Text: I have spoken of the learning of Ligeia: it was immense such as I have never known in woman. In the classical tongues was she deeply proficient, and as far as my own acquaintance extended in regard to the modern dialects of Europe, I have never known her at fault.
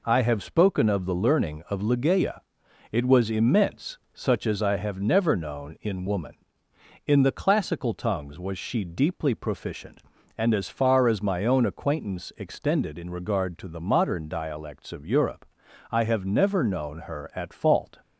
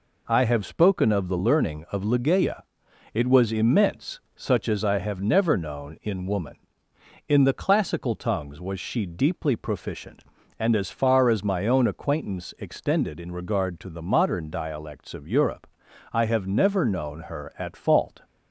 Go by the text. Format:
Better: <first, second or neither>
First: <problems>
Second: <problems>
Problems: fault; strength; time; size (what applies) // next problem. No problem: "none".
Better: neither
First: none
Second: none